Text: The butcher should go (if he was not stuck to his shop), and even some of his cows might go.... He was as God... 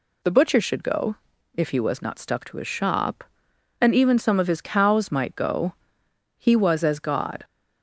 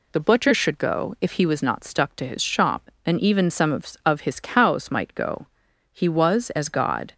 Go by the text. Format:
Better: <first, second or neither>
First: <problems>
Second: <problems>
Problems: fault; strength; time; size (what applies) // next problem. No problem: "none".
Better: first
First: none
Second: says "of" twice; at 4.0 s